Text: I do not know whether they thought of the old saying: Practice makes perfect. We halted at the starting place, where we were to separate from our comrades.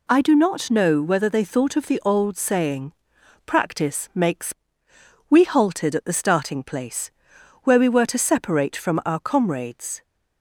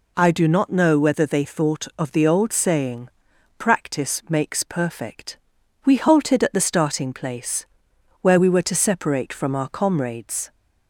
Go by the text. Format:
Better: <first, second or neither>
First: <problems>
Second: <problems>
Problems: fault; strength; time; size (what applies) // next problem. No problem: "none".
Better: second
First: skips "perfect"; at 4.9 s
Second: none